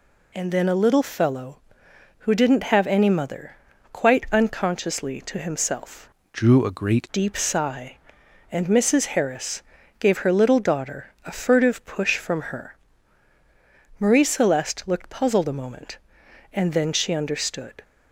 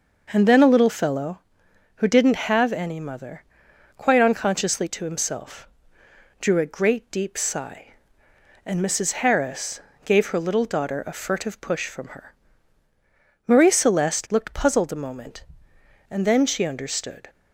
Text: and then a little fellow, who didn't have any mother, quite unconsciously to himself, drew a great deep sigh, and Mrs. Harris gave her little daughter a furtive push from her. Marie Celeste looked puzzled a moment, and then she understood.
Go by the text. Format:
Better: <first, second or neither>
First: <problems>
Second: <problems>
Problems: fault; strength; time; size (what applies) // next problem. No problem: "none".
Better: second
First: changes voice from "drew" to "great"; from 6.3 to 7.0 s; 0.7 s long // pauses between "Harris" and "gave"; at 9.6 s; 0.38 s long // pauses between "daughter" and "a"; slight; at 11.0 s; 0.16 s long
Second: pauses between "Harris" and "gave"; slight; at 9.8 s; 0.24 s long